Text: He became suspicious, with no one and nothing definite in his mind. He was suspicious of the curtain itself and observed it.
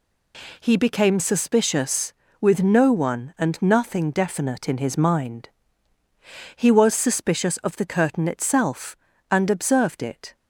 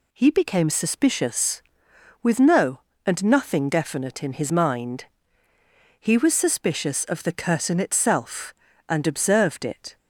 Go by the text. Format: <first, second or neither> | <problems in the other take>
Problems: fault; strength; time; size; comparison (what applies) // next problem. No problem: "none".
first | skips "one"; at 2.9 s